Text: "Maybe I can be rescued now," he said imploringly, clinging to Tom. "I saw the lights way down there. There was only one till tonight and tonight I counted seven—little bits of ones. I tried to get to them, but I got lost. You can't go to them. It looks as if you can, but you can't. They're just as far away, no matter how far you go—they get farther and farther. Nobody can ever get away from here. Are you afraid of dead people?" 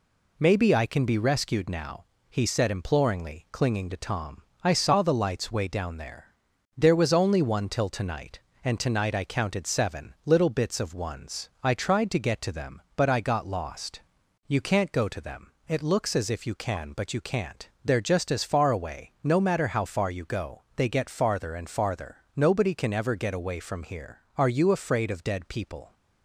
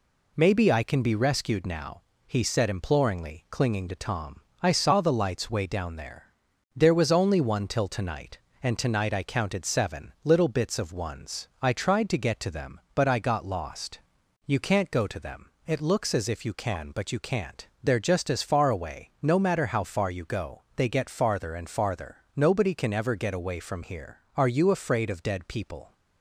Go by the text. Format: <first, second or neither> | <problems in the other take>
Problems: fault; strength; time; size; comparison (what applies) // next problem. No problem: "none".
neither | none